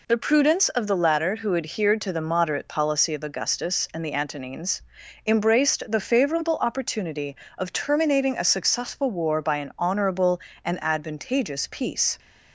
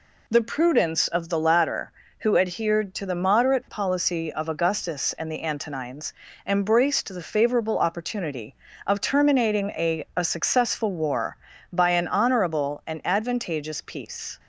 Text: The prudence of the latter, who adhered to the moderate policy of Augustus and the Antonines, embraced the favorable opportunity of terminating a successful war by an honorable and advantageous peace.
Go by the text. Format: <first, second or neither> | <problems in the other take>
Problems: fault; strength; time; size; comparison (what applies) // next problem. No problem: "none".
first | says "a" twice; at 10.1 s